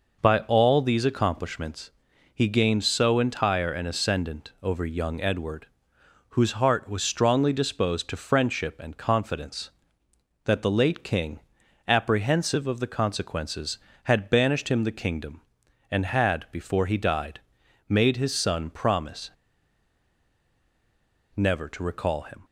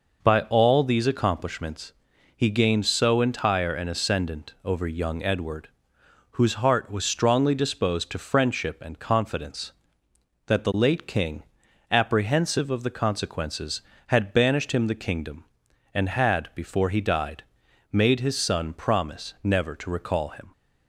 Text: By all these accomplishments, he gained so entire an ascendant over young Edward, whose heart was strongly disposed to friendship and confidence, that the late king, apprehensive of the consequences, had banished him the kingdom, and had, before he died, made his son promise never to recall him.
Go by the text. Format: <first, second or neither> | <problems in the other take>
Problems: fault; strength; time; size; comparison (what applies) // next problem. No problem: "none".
second | pauses between "promise" and "never"; strong; at 19.3 s; 2.0 s long